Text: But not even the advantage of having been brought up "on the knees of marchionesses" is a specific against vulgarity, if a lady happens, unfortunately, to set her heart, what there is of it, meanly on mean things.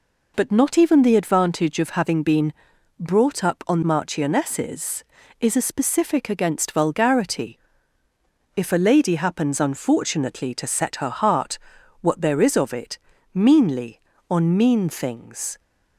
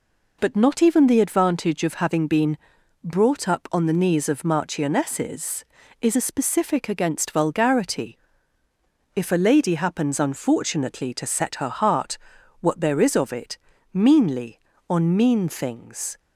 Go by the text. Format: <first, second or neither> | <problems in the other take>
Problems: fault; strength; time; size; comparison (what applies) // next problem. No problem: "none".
second | pauses between "been" and "brought"; noticeable; at 2.5 s; 0.46 s long; noticeable in the second // skips "the knees of"; at 3.8 s